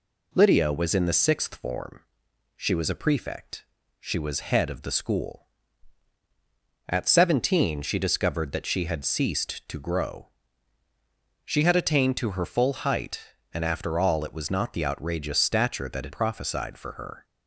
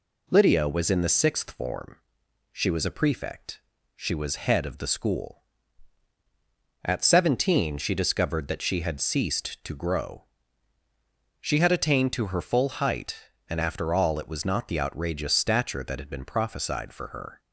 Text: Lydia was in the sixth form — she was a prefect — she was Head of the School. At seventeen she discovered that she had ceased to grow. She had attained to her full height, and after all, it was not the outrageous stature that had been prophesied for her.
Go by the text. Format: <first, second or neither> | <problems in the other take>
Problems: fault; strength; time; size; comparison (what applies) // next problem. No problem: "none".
second | skips "been"; at 16.1 s